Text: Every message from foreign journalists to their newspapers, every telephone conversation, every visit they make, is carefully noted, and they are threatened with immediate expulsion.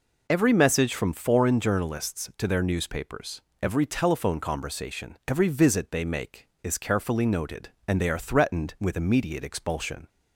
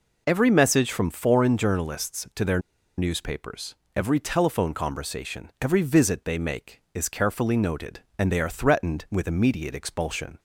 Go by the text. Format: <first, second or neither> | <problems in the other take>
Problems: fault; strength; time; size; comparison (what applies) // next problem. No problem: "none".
first | pauses between "their" and "newspapers"; at 2.6 s; 0.37 s long